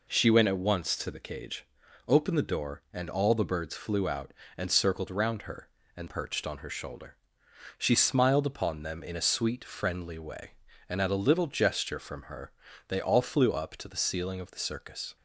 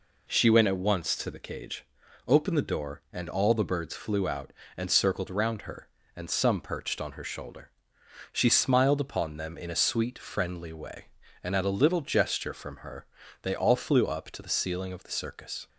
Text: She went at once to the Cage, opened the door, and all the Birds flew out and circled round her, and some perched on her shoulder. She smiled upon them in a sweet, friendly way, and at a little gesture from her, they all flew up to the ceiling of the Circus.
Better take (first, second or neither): second